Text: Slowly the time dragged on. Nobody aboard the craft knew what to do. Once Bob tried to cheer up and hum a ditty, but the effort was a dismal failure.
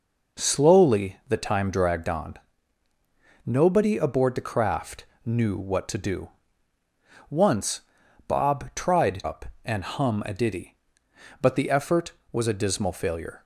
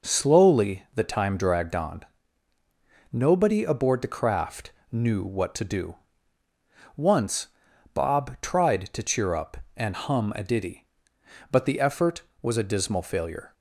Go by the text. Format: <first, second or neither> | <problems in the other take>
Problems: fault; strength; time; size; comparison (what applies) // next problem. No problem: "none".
second | pauses between "craft" and "knew"; slight; at 5.0 s; 0.20 s long; slight in the second // pauses between "Once" and "Bob"; noticeable; at 7.8 s; 0.48 s long; noticeable in the second // skips "to cheer"; at 9.2 s